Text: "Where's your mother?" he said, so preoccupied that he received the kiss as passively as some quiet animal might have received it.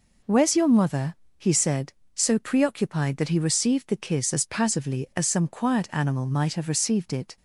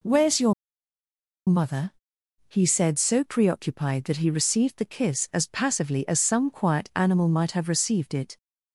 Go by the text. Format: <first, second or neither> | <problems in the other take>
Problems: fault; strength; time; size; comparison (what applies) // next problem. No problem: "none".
first | pauses between "your" and "mother"; noticeable; at 0.5 s; 0.95 s long